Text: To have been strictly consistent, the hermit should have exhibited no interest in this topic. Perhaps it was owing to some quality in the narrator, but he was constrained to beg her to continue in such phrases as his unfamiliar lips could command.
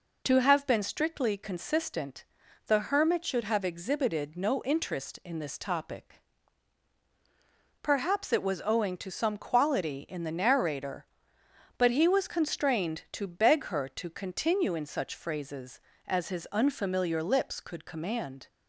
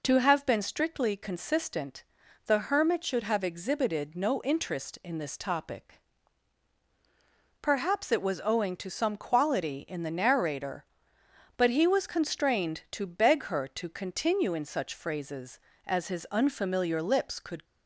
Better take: first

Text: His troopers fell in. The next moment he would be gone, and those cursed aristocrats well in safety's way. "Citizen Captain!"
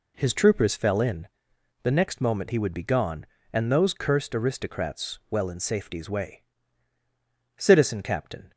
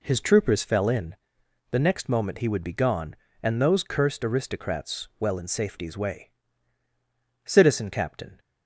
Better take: neither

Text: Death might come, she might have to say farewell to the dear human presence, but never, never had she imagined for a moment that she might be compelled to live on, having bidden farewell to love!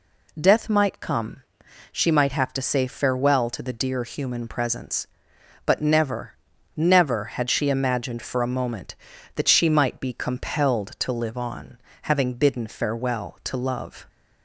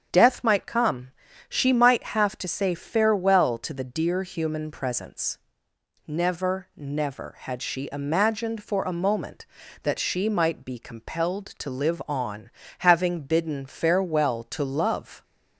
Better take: first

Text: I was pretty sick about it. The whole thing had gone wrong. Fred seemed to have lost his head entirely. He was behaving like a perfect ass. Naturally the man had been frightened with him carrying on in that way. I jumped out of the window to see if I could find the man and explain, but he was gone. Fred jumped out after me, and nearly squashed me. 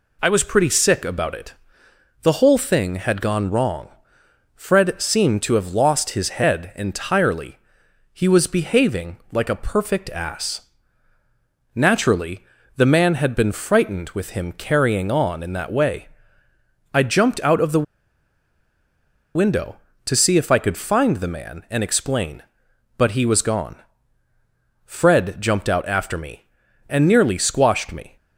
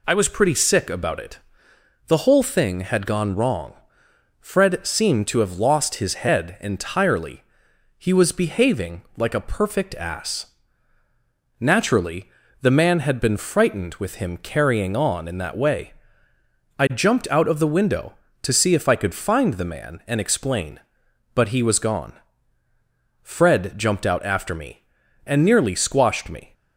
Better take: second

